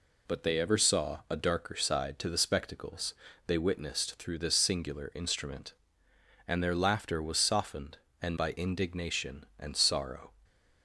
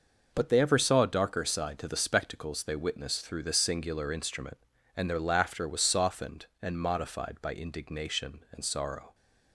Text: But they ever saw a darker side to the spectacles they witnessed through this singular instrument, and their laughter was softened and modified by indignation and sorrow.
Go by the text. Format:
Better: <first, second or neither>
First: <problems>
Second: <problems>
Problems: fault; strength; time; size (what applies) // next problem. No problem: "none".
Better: second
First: pauses between "spectacles" and "they"; slight; at 3.1 s; 0.34 s long // skips "modified"; at 8.3 s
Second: none